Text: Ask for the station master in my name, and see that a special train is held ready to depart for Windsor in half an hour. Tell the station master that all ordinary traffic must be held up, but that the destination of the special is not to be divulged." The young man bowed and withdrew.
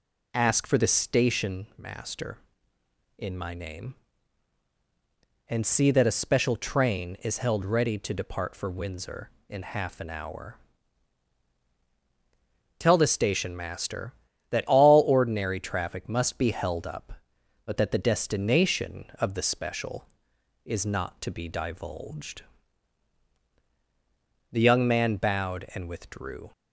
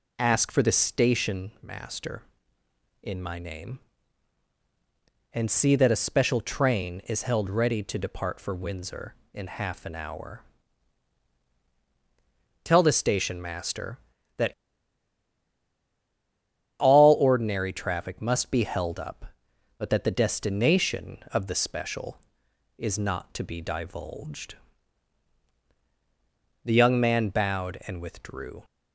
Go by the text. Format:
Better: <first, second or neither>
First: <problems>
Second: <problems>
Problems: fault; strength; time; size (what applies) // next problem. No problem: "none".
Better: first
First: none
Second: pauses between "that" and "all"; strong; at 14.5 s; 2.2 s long